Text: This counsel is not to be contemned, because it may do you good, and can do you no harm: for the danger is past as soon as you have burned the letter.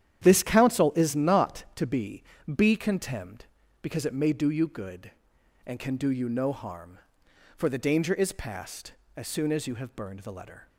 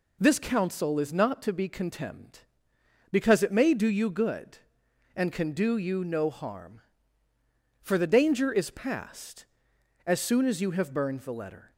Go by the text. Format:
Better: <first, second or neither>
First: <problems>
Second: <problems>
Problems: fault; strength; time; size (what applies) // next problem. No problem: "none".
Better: second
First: starts louder than the rest; strong; until 1.2 s; 10 dB // says "be" twice; at 2.5 s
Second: none